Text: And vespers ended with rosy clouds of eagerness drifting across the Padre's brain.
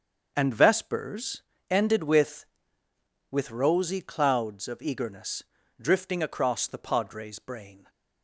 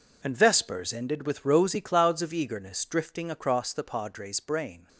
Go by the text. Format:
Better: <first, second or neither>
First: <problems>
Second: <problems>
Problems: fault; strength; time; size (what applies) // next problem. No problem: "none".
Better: second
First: starts louder than the rest; until 1.3 s; 6.5 dB // pauses between "vespers" and "ended"; slight; at 1.4 s; 0.28 s long // says "with" twice; at 3.3 s // pauses between "eagerness" and "drifting"; slight; at 5.4 s; 0.36 s long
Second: none